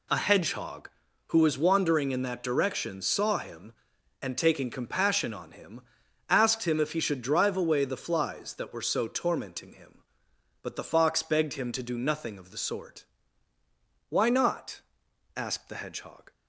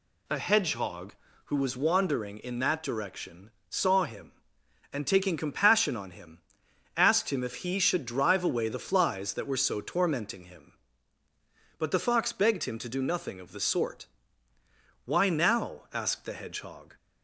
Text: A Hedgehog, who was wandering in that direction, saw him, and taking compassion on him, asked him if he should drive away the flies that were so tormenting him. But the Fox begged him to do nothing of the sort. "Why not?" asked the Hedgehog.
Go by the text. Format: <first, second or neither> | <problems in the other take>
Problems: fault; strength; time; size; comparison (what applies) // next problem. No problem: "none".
first | says "now" for "not"; at 15.2 s